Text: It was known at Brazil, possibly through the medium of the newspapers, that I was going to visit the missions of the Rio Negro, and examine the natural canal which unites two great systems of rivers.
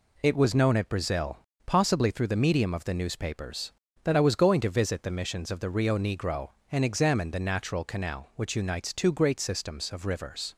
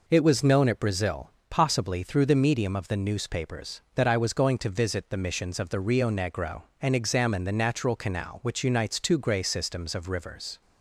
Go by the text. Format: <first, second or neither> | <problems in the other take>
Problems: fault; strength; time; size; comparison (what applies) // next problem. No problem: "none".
first | says "grey" for "great"; at 9.1 s